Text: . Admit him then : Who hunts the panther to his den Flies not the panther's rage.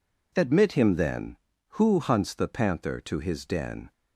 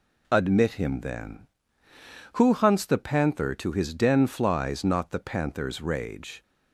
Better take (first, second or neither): second